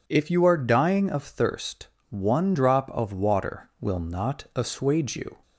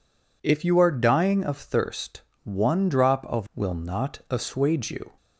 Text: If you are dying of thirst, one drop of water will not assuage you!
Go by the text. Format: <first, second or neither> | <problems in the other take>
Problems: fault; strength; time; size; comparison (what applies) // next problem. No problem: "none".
first | skips "water"; at 3.5 s